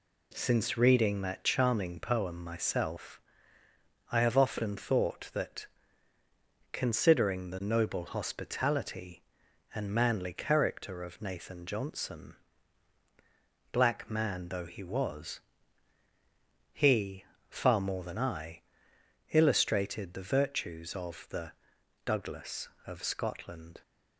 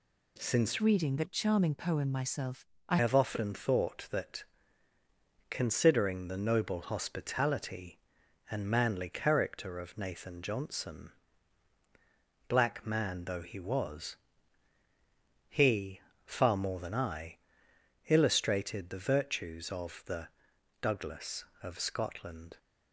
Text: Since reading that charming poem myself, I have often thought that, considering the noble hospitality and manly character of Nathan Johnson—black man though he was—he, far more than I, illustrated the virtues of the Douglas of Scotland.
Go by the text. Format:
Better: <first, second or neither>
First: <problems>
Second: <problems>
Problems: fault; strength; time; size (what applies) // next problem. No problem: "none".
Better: first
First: pauses between "the" and "Douglas"; noticeable; at 21.5 s; 0.54 s long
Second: changes voice from "reading" to "I"; from 0.7 to 2.9 s; 2.2 s long // pauses between "the" and "Douglas"; noticeable; at 20.2 s; 0.54 s long